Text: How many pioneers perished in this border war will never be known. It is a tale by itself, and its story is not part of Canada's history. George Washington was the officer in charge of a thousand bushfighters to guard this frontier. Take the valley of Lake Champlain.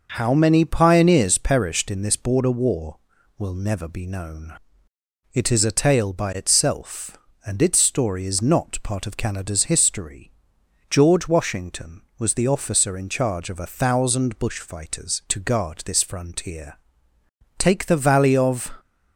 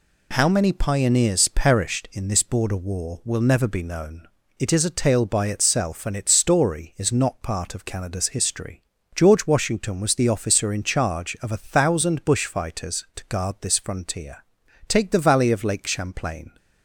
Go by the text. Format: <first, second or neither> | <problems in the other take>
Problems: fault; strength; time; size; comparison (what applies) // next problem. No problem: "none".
second | stops before "Lake Champlain"; at 18.7 s